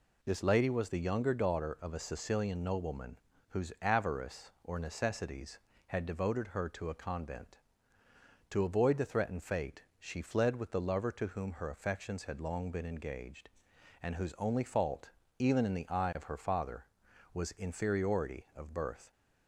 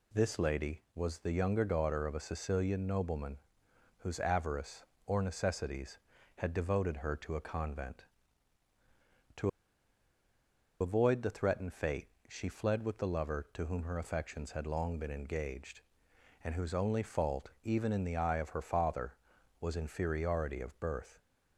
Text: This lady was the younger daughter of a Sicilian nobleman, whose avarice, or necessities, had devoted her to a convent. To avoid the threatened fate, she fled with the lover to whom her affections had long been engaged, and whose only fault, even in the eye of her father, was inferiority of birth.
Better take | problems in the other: first | pauses between "To" and "avoid"; strong; at 9.4 s; 1.3 s long

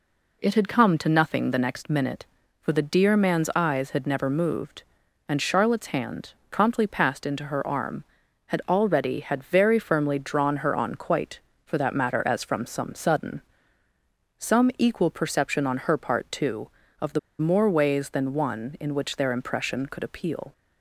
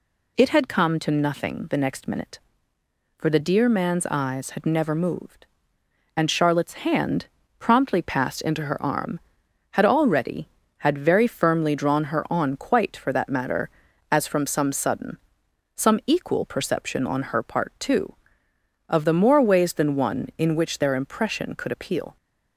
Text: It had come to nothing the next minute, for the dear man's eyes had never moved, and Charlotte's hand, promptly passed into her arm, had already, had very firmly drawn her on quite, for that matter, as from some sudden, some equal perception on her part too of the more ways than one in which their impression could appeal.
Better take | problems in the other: second | pauses between "the" and "more"; slight; at 17.1 s; 0.20 s long

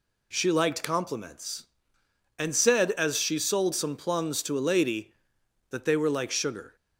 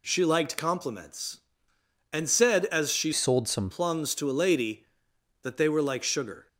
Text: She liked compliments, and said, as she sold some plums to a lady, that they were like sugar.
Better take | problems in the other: first | changes voice from "sold" to "some"; from 3.1 to 3.6 s; 0.5 s long

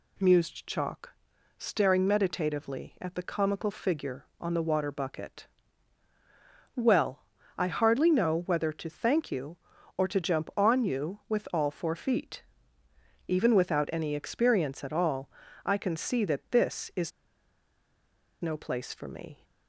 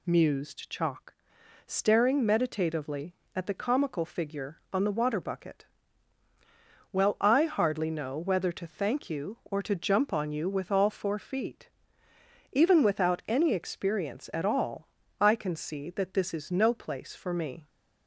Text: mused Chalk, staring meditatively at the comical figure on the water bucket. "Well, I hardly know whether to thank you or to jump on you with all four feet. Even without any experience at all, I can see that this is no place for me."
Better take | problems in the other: second | pauses between "is" and "no"; strong; at 17.1 s; 1.3 s long

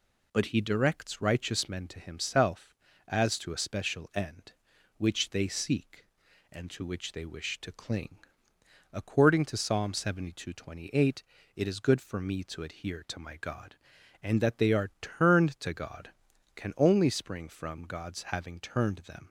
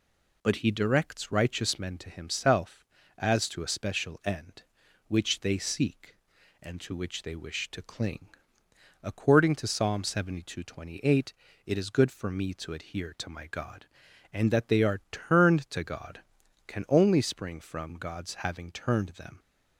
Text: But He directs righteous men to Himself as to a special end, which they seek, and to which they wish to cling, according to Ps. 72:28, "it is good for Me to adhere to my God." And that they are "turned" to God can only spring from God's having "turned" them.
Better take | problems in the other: neither | none

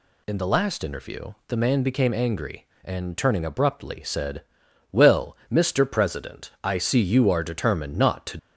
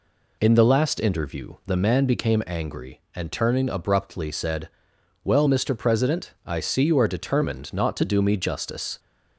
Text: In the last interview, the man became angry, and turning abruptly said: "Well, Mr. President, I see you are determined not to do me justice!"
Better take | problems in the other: second | stops before "do me justice"; at 8.3 s

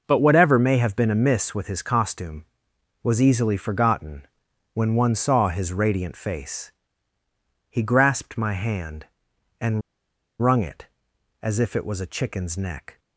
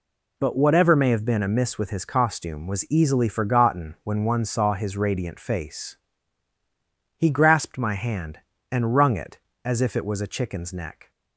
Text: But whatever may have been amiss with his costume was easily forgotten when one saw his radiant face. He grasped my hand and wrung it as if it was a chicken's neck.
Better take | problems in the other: second | pauses between "forgotten" and "when"; noticeable; at 4.2 s; 0.48 s long // pauses between "and" and "wrung"; noticeable; at 9.8 s; 0.59 s long

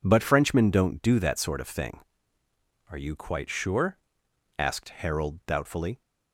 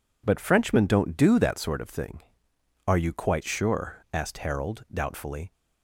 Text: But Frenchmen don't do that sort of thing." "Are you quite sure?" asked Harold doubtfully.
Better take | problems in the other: neither | none

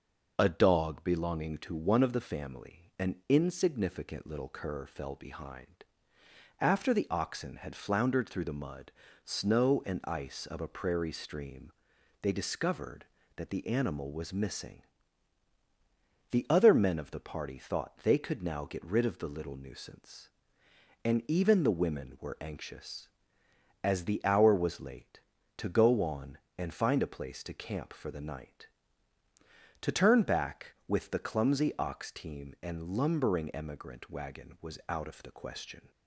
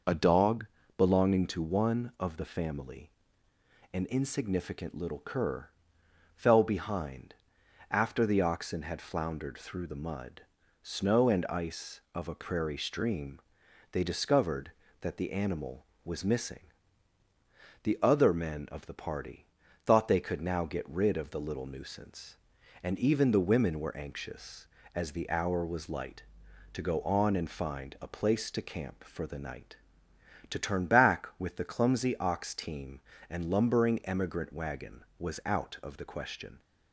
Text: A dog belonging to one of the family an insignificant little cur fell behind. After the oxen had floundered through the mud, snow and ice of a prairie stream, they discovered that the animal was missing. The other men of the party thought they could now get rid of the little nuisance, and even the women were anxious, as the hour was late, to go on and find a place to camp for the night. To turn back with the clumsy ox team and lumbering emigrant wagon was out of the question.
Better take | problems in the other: first | pauses between "dog" and "belonging"; slight; at 0.6 s; 0.32 s long // pauses between "family" and "an"; noticeable; at 3.0 s; 0.84 s long // pauses between "cur" and "fell"; noticeable; at 5.6 s; 0.66 s long // pauses between "party" and "thought"; at 19.4 s; 0.40 s long // says "light" for "late"; at 25.8 s

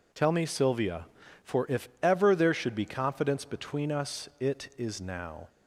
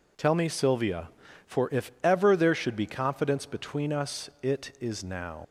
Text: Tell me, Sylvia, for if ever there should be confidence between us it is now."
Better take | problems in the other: first | leaves "now" unfinished; at 5.4 s; 60 ms

